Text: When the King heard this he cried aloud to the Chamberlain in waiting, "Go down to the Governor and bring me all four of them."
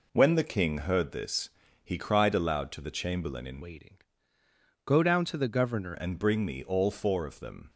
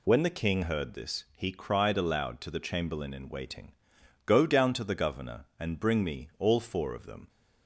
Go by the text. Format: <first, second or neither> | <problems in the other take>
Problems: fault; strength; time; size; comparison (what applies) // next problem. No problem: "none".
second | pauses between "this" and "he"; slight; at 1.4 s; 0.34 s long // changes voice from "waiting" to "Governor"; from 3.6 to 5.9 s; 2.3 s long